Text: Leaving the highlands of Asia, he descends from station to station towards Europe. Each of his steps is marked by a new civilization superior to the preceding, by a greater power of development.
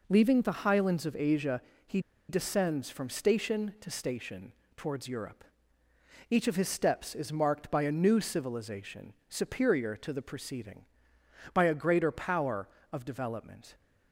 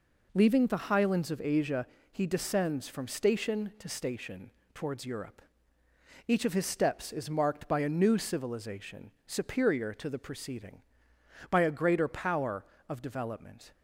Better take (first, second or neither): second